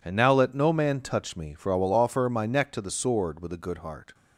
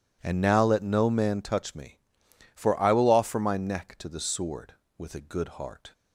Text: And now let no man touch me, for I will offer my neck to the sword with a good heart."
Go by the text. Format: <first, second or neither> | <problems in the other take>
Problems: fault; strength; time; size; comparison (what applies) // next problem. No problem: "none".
neither | none